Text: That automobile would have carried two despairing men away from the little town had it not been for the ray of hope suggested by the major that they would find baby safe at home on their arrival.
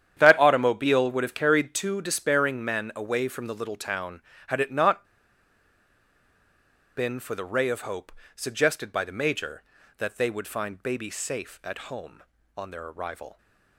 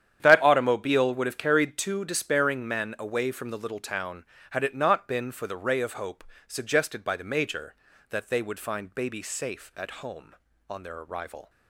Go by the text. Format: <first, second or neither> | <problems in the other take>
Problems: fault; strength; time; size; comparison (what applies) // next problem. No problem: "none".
second | starts louder than the rest; strong; until 1.1 s; 9.5 dB; strong in the second // pauses between "not" and "been"; strong; at 5.0 s; 1.9 s long // pauses between "hope" and "suggested"; slight; at 8.1 s; 0.24 s long; slight in the second